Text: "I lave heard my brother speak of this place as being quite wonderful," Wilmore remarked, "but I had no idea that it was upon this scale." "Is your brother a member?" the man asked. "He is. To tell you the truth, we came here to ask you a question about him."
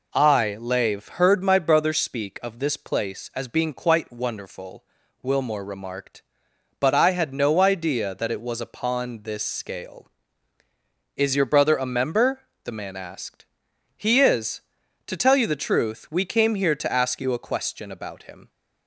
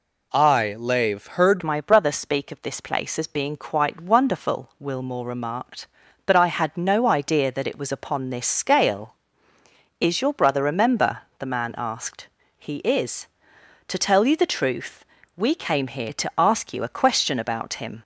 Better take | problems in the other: first | changes voice at "my"; from 1.6 s on; 16.4 s long

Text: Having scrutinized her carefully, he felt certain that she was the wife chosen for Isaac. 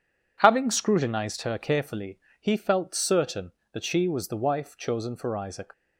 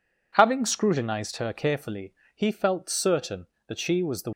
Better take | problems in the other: first | stops before "wife chosen for Isaac"; at 4.3 s

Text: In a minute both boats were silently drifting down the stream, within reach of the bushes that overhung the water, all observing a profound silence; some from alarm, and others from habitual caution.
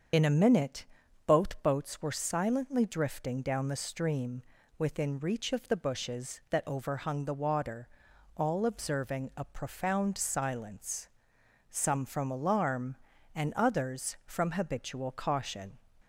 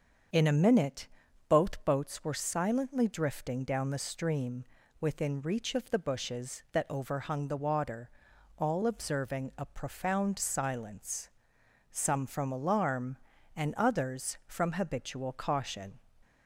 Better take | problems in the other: second | loses the start of "In"; at 0.1 s; 30 ms // starts louder than the rest; until 1.5 s; 7 dB; also in the second // pauses between "minute" and "both"; at 0.8 s; 0.40 s long; also in the second

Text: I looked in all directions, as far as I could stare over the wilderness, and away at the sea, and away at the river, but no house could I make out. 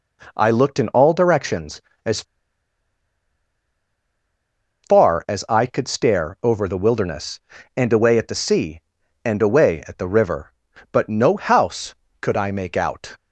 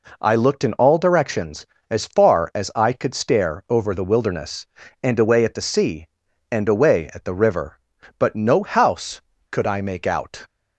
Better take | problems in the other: second | pauses between "as" and "far"; strong; at 2.2 s; 2.6 s long

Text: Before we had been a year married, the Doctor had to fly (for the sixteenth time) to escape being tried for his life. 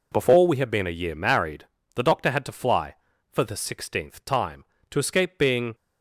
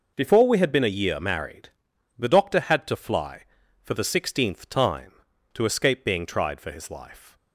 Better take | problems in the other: second | stops before "tried for his life"; at 5.7 s

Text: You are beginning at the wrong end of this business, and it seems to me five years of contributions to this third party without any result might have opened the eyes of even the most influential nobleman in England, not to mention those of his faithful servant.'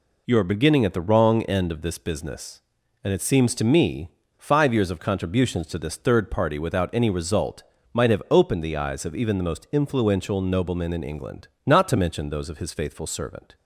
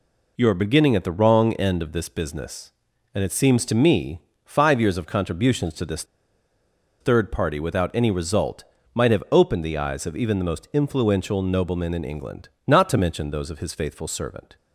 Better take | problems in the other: first | pauses between "me" and "five"; slight; at 4.2 s; 0.24 s long; slight in the first // pauses between "this" and "third"; noticeable; at 6.0 s; 0.96 s long // pauses between "result" and "might"; slight; at 8.6 s; 0.30 s long; slight in the first

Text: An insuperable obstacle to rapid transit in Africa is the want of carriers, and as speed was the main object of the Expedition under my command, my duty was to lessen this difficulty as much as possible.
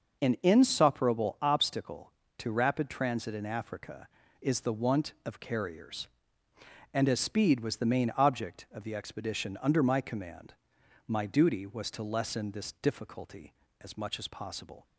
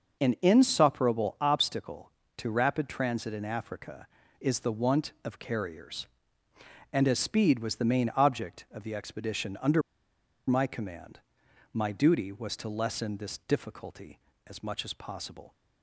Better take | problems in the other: first | pauses between "under" and "my"; noticeable; at 9.8 s; 0.66 s long

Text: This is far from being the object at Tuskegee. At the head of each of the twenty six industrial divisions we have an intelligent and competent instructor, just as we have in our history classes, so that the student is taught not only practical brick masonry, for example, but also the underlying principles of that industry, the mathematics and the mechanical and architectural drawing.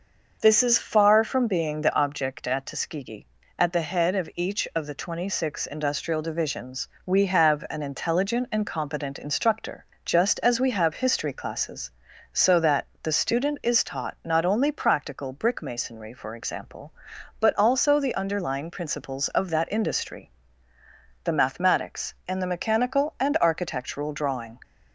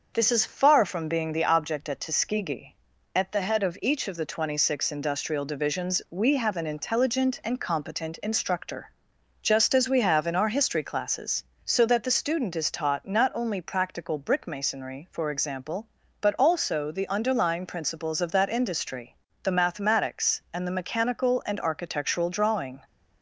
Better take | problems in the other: second | starts louder than the rest; noticeable; until 1.4 s; 6 dB; also in the second // pauses between "divisions" and "we"; slight; at 6.8 s; 0.18 s long // skips "in our"; at 10.9 s // pauses between "that" and "the"; slight; at 12.8 s; 0.16 s long

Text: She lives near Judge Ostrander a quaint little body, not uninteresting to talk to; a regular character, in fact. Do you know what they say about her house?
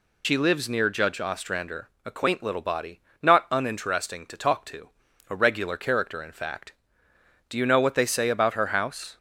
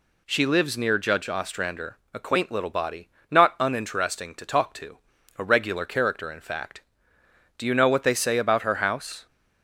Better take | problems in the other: second | loses the start of "She"; at 0.2 s; 75 ms // pauses between "Ostrander" and "a"; slight; at 1.8 s; 0.16 s long; slight in the second

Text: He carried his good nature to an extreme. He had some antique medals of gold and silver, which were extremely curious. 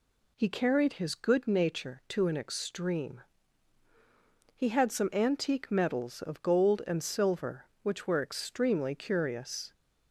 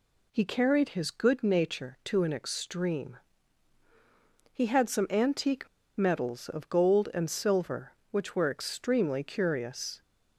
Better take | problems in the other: first | pauses between "antique" and "medals"; slight; at 5.6 s; 0.29 s long

